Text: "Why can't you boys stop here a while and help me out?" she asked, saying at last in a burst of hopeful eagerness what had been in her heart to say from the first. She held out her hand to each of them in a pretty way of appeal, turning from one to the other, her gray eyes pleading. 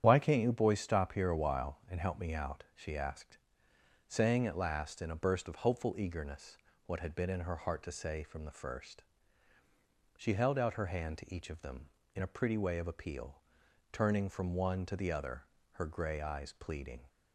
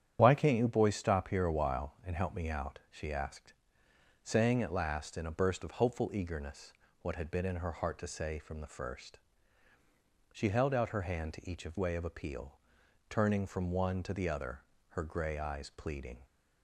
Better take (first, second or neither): first